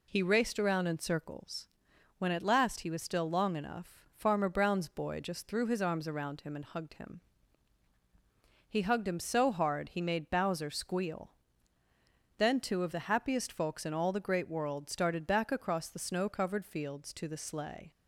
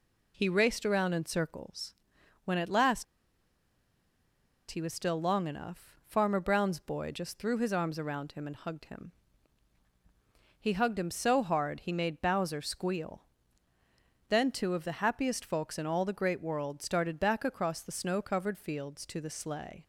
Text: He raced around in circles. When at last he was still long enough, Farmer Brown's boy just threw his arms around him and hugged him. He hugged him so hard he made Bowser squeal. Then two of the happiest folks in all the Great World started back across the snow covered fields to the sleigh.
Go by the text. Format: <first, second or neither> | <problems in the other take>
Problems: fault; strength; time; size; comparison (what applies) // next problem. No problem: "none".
first | pauses between "last" and "he"; strong; at 3.0 s; 1.6 s long